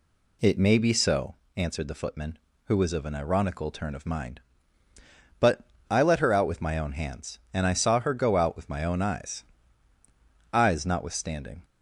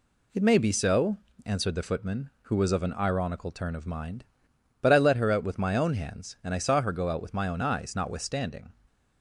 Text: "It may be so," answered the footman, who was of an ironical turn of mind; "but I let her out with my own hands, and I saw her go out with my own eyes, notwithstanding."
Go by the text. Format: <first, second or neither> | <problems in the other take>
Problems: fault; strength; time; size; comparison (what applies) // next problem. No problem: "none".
second | pauses between "but" and "I"; slight; at 5.6 s; 0.22 s long // says "eyes" twice; at 10.5 s